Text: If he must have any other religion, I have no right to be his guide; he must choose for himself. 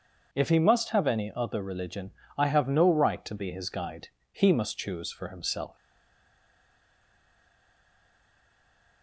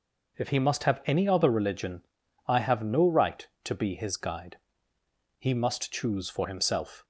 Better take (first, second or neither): second